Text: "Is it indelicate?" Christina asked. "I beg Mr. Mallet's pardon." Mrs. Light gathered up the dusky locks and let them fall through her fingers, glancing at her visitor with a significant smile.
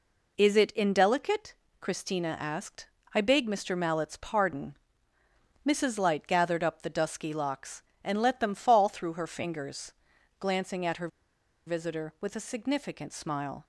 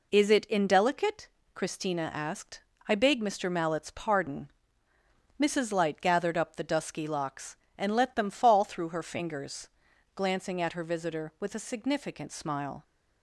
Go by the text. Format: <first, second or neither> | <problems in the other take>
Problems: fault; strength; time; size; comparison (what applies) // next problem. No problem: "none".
second | pauses between "her" and "visitor"; noticeable; at 11.0 s; 0.59 s long